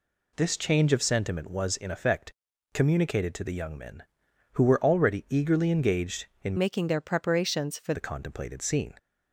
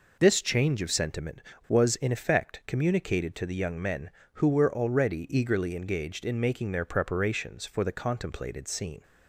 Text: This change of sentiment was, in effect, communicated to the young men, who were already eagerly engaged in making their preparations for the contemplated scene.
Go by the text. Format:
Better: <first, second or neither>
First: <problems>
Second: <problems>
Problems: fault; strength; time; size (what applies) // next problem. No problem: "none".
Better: second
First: changes voice from "making" to "for"; from 6.5 to 7.9 s; 1.4 s long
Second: none